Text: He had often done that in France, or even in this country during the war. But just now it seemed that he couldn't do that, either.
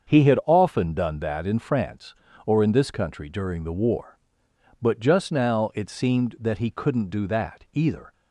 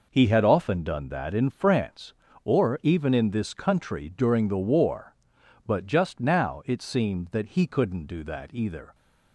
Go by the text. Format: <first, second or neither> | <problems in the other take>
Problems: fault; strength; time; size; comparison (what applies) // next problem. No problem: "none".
second | starts louder than the rest; until 1.1 s; 7 dB // skips "even"; at 2.6 s